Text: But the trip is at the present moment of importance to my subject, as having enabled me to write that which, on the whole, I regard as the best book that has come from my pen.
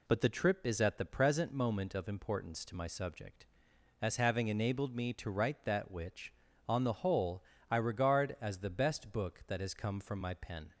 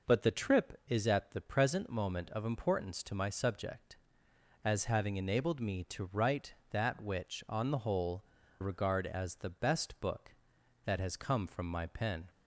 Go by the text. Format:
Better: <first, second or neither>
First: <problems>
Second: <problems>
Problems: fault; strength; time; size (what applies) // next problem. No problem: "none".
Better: first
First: none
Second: skips "I"; at 8.4 s